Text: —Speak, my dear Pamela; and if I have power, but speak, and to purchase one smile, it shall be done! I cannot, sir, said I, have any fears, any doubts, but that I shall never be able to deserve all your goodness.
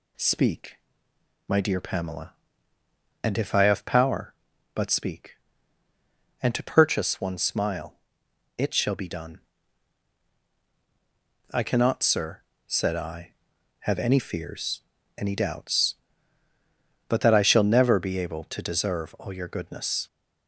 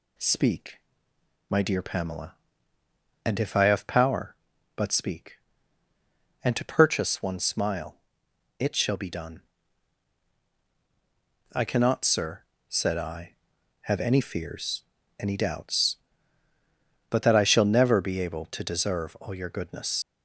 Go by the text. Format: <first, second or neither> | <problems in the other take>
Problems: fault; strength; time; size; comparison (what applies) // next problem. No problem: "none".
first | leaves "goodness" unfinished; at 20.0 s; 60 ms